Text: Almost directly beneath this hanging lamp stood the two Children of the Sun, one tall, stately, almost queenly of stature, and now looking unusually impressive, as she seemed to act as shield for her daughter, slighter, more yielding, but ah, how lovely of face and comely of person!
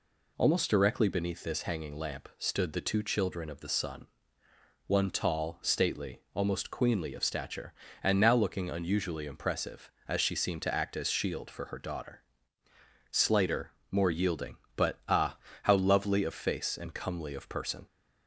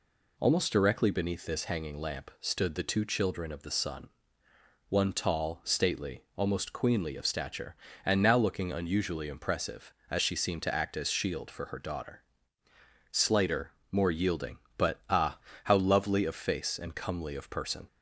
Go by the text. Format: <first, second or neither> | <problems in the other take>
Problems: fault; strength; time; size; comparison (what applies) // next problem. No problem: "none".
neither | none